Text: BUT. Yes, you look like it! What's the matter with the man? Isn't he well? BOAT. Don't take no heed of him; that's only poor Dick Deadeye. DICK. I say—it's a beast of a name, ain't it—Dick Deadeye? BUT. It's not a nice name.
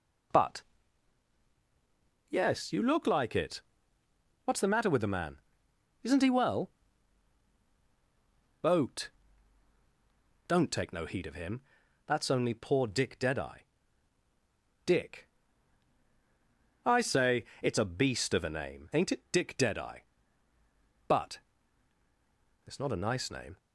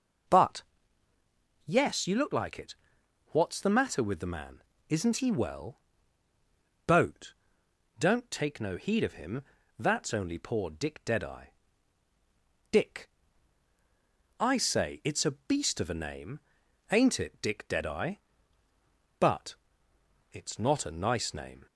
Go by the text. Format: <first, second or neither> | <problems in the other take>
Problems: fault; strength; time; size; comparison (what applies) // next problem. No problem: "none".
neither | none